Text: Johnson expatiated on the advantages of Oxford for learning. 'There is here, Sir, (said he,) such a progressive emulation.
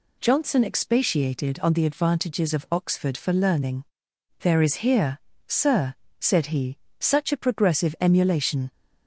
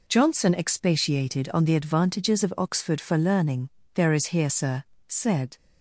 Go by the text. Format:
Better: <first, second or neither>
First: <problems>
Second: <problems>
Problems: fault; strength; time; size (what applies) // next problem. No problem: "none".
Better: first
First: none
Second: stops before "he such a progressive emulation"; at 5.5 s